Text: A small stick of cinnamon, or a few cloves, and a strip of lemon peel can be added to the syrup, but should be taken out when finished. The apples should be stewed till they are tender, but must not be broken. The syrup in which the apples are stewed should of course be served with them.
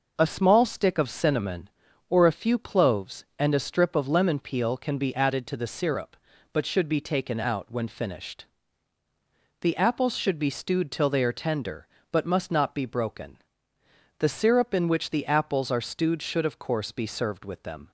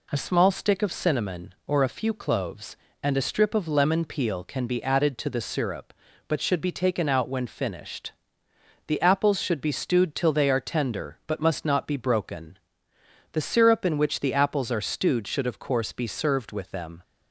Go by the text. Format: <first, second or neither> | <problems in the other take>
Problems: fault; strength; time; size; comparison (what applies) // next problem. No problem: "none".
neither | none